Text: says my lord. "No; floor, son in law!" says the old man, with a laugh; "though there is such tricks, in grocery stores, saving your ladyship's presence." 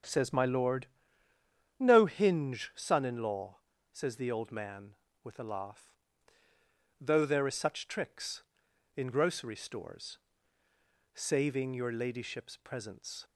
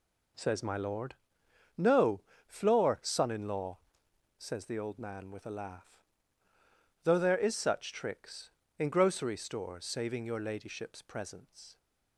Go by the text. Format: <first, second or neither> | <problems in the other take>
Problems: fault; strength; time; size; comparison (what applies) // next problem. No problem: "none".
second | starts louder than the rest; strong; until 1.9 s; 8 dB // says "hinge" for "floor"; at 2.0 s